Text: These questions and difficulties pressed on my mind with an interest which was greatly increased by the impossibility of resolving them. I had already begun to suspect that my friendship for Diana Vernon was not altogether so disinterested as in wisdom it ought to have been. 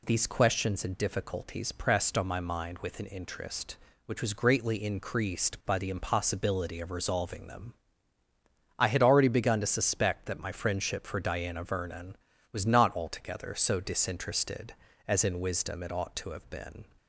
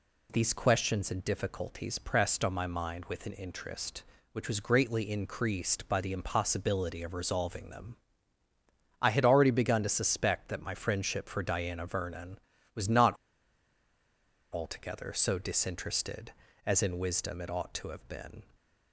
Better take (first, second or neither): first